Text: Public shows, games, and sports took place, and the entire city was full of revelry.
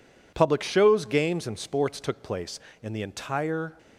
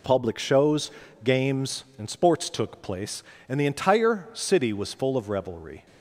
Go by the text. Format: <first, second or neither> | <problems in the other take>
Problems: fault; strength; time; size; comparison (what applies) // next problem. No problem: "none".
second | stops before "city was full of revelry"; at 3.7 s